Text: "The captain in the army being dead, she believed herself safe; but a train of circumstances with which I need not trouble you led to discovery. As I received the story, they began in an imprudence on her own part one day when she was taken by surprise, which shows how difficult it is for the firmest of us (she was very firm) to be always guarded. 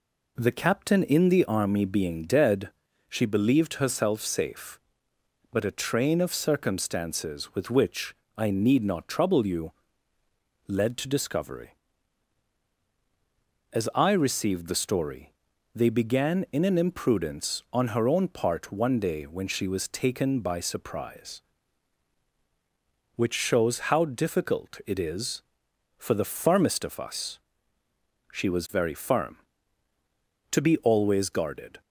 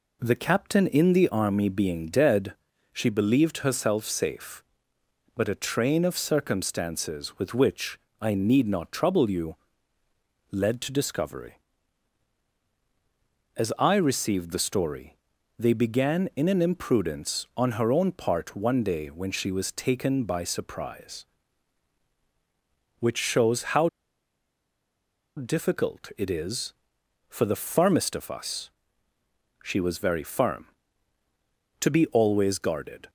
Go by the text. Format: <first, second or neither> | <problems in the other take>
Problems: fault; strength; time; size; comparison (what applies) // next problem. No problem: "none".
first | pauses between "which" and "I"; slight; at 7.9 s; 0.22 s long; slight in the first // pauses between "you" and "led"; noticeable; at 9.5 s; 0.94 s long; noticeable in the first // pauses between "how" and "difficult"; strong; at 23.8 s; 1.4 s long